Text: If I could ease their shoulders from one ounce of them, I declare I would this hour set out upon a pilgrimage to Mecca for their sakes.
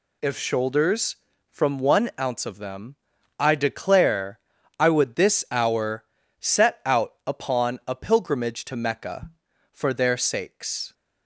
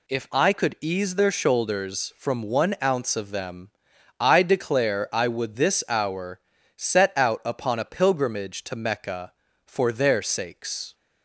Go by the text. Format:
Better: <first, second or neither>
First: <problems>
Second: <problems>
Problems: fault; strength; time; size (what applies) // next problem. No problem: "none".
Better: second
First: skips "I could ease their"; at 0.3 s // pauses between "declare" and "I"; at 4.3 s; 0.42 s long // pauses between "hour" and "set"; slight; at 6.0 s; 0.36 s long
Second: pauses between "hour" and "set"; slight; at 6.4 s; 0.36 s long